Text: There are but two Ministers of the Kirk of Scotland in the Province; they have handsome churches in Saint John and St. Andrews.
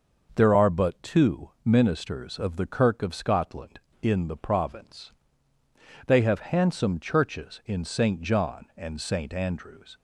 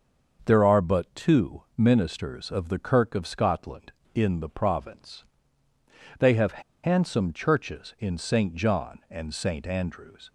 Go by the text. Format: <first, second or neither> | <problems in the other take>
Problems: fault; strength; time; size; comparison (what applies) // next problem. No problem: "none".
first | starts louder than the rest; until 1.4 s; 6.5 dB; noticeable in the first // pauses between "have" and "handsome"; slight; at 6.6 s; 0.21 s long